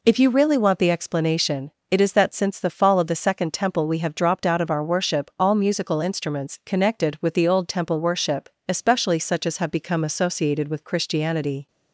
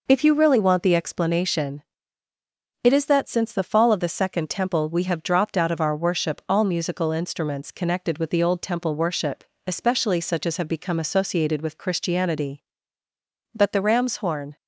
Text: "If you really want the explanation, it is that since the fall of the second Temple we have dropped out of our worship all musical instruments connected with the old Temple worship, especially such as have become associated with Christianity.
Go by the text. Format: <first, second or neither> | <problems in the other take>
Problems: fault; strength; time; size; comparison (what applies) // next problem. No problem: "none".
first | goes on to say "But the ram's horn"; noticeable; from 13.5 s on; 1.0 s long